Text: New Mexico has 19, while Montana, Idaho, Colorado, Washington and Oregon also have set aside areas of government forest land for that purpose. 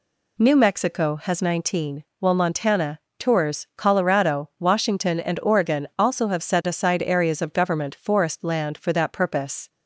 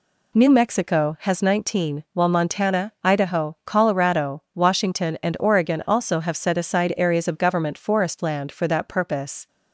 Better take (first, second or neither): second